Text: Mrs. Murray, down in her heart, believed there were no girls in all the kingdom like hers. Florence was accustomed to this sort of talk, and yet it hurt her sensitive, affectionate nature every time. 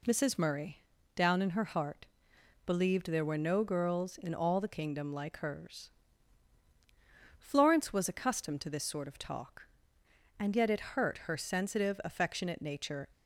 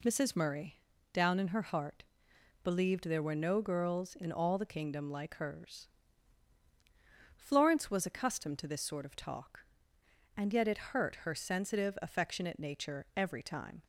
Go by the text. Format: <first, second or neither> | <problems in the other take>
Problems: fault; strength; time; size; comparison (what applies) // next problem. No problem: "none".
second | stops before "every time"; at 13.1 s